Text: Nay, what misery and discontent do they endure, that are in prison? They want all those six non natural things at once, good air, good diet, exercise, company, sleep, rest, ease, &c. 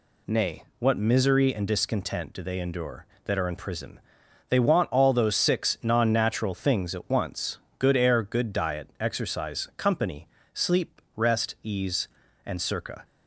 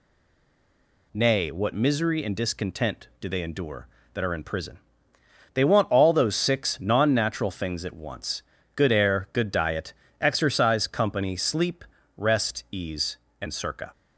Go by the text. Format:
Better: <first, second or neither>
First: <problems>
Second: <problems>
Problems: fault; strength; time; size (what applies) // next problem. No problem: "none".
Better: first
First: none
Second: stays silent before the first word; until 1.1 s; 1.1 s long